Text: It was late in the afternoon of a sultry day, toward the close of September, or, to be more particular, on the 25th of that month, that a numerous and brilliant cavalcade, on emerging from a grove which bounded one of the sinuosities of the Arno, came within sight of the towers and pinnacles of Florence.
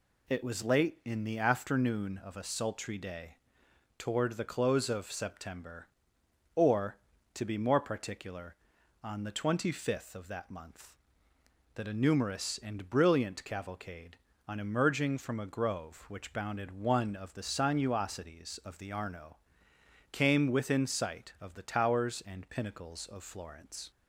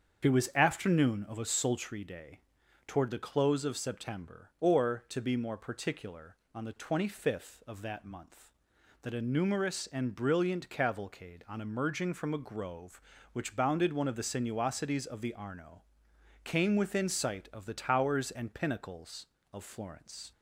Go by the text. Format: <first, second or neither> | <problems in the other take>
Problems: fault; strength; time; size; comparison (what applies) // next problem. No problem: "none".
first | starts louder than the rest; strong; until 1.3 s; 7 dB // skips "late in the"; at 0.5 s